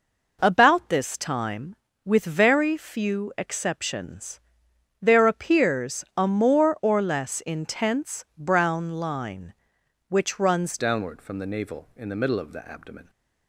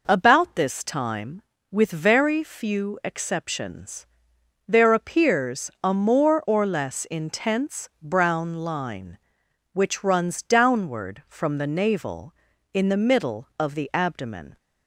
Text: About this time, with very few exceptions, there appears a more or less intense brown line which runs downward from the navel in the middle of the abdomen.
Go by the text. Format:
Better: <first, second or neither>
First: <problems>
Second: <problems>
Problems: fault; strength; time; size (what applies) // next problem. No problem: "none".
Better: second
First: changes voice at "downward"; from 10.7 s on; 2.3 s long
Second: none